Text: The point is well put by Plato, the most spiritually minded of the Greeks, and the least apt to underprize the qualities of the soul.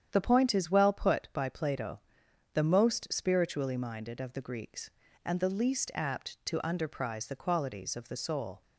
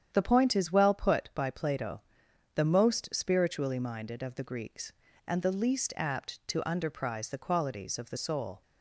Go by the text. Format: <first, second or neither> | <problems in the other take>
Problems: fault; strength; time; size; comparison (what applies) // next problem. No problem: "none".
neither | starts louder than the rest; strong; the same in both